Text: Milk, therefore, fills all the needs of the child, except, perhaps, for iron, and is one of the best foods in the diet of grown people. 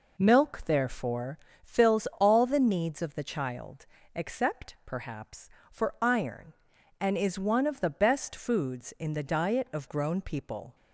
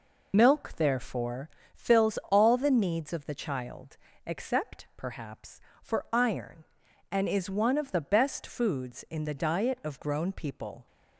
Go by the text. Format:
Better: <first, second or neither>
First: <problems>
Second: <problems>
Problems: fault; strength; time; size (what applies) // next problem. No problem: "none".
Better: first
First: none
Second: loses the start of "Milk"; at 0.3 s; 40 ms